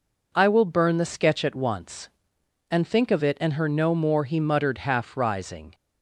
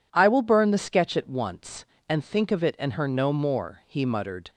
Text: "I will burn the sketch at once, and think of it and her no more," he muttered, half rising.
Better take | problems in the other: first | stops before "half rising"; at 4.4 s

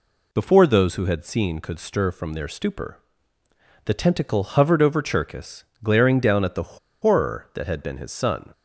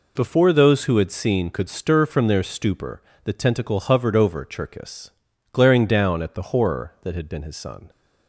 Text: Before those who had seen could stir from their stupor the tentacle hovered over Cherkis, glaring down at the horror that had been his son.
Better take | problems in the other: second | pauses between "stupor" and "the"; noticeable; at 2.9 s; 0.88 s long; slight in the second // pauses between "the" and "horror"; slight; at 6.7 s; 0.24 s long

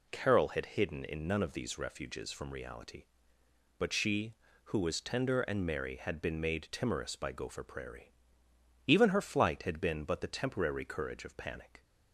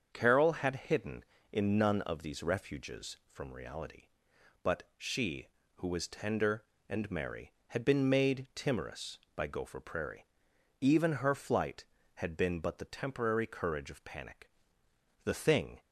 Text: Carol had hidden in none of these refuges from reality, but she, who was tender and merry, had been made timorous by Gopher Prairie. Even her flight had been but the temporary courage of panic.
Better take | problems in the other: first | starts louder than the rest; until 1.1 s; 7 dB // goes on to say "The thing"; from 15.2 s on; 0.56 s long

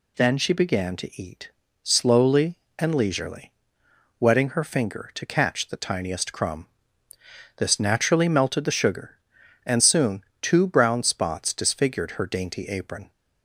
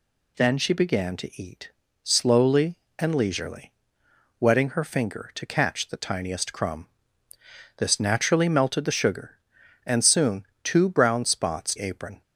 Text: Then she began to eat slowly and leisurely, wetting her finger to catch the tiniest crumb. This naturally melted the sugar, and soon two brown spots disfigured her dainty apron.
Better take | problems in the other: first | pauses between "eat" and "slowly"; slight; at 1.7 s; 0.32 s long; slight in the first // pauses between "soon" and "two"; slight; at 10.4 s; 0.18 s long; slight in the first // skips "disfigured her dainty"; at 11.7 s

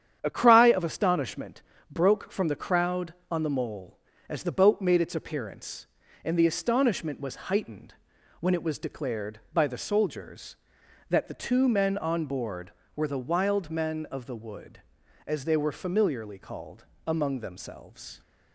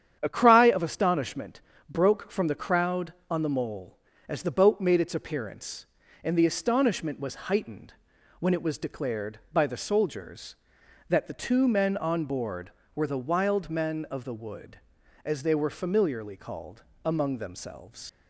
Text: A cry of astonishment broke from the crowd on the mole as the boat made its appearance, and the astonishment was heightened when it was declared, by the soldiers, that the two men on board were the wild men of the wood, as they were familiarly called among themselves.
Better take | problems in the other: first | starts louder than the rest; strong; until 1.2 s; 9 dB; strong in the first // pauses between "astonishment" and "broke"; slight; at 1.6 s; 0.28 s long; slight in the first // pauses between "heightened" and "when"; noticeable; at 7.9 s; 0.48 s long; noticeable in the first // pauses between "called" and "among"; slight; at 16.8 s; 0.22 s long; slight in the first // leaves "themselves" unfinished; at 18.0 s; 95 ms

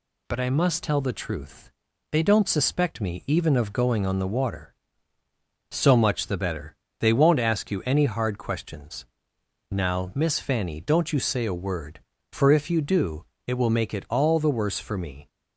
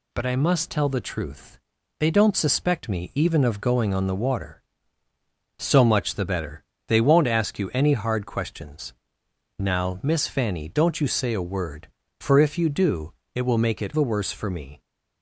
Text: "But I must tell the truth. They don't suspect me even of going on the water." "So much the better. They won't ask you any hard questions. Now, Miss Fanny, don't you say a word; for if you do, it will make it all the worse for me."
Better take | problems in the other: first | skips "all"; at 13.9 s

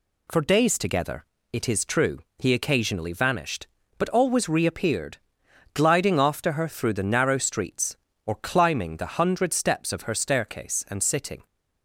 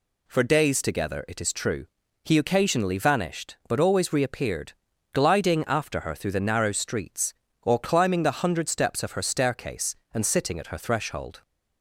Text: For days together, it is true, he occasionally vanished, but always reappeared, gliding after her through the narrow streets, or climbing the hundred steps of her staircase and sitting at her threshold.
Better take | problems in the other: second | stops before "at her threshold"; at 11.4 s

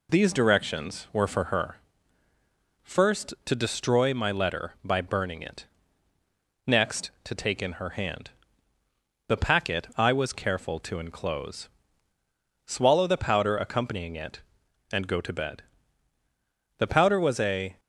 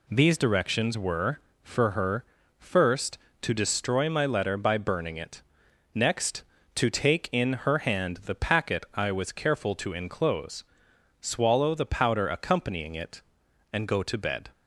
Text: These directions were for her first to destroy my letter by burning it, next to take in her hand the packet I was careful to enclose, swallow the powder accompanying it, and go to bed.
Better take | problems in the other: second | pauses between "her" and "first"; at 1.7 s; 1.0 s long; slight in the second // pauses between "hand" and "the"; noticeable; at 8.3 s; 0.98 s long // goes on to say "The powder was a"; noticeable; from 16.7 s on; 1.0 s long

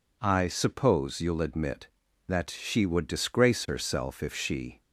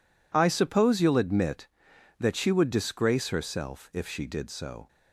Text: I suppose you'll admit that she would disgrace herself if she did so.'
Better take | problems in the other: second | stops before "did so"; at 4.8 s

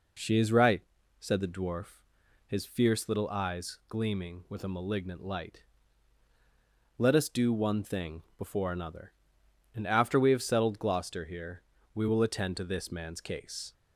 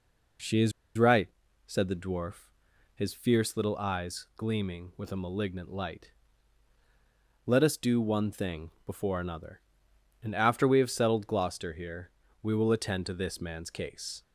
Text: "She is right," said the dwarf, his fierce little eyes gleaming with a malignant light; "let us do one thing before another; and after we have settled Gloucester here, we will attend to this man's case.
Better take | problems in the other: first | pauses between "is" and "right"; slight; at 0.7 s; 0.26 s long // pauses between "thing" and "before"; slight; at 8.7 s; 0.16 s long; slight in the first

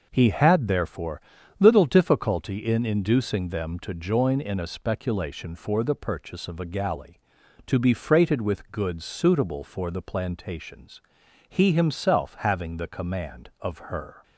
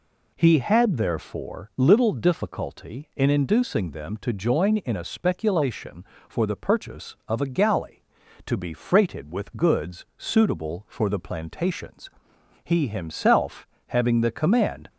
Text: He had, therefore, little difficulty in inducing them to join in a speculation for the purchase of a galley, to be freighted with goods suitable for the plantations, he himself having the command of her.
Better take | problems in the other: first | pauses between "himself" and "having"; slight; at 13.6 s; 0.20 s long // stops before "of her"; at 14.8 s

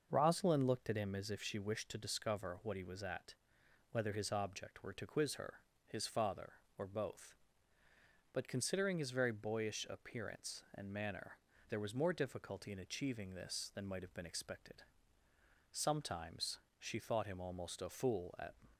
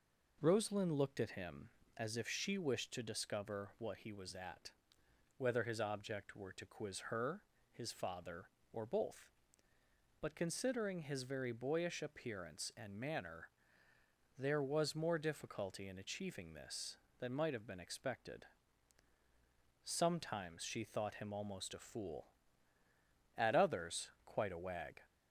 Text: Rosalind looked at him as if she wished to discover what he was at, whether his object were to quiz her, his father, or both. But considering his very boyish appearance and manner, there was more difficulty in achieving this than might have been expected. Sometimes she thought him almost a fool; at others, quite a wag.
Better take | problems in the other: second | starts louder than the rest; noticeable; until 1.1 s; 6 dB // pauses between "Sometimes" and "she"; slight; at 16.5 s; 0.22 s long // stops before "others quite a wag"; at 18.7 s

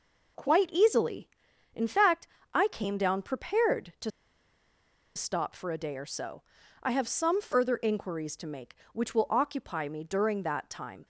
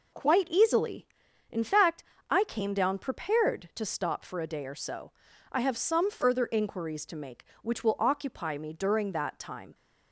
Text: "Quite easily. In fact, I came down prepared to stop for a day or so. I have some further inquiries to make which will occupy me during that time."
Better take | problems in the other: second | pauses between "to" and "stop"; at 4.0 s; 1.0 s long

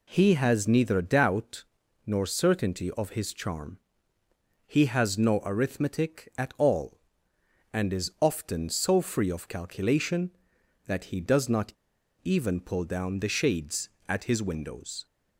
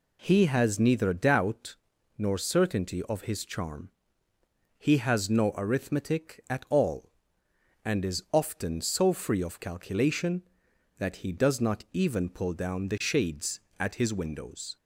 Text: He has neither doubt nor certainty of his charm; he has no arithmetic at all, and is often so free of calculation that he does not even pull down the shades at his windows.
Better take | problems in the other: second | pauses between "doubt" and "nor"; at 1.6 s; 0.42 s long; also in the second // pauses between "not" and "even"; noticeable; at 11.7 s; 0.52 s long

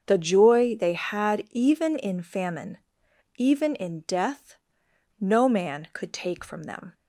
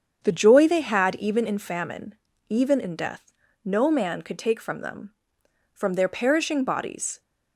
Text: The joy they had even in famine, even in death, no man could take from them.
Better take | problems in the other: first | starts louder than the rest; strong; until 1.2 s; 7.5 dB; also in the first // goes on to say "From their perishing bodies"; from 5.7 s on; 1.4 s long

